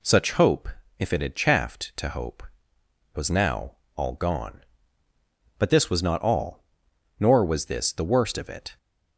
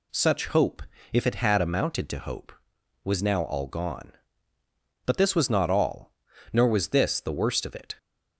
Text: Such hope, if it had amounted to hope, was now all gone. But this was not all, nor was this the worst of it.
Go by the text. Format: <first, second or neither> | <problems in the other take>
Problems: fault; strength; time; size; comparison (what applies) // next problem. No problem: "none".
second | says "chaffed" for "amounted"; at 1.3 s // pauses between "now" and "all"; slight; at 3.7 s; 0.22 s long